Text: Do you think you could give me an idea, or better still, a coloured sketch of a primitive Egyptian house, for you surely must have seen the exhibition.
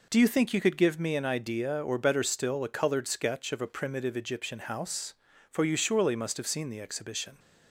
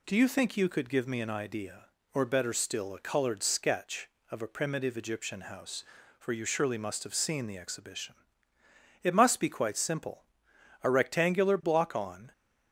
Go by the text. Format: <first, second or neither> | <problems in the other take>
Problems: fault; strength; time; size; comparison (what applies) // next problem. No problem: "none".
first | goes on to say "It must be quite simple a rectangular block on"; strong; from 9.0 s on; 3.3 s long